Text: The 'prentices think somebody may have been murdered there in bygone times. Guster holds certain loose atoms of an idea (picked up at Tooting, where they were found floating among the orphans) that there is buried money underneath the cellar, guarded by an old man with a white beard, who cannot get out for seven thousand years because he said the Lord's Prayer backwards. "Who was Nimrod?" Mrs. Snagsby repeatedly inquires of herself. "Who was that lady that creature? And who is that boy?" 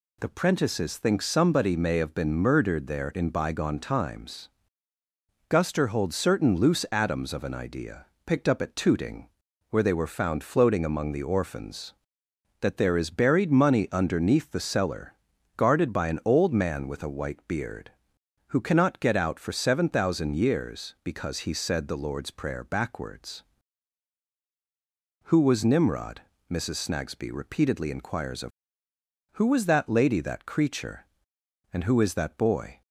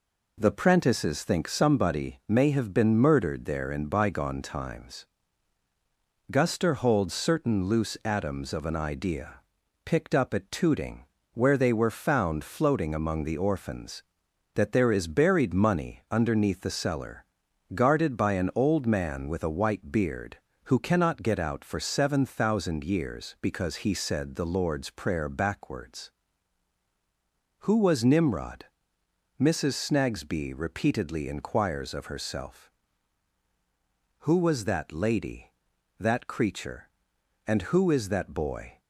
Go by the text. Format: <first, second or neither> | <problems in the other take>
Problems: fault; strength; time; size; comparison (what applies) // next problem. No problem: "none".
second | skips "herself"; at 28.9 s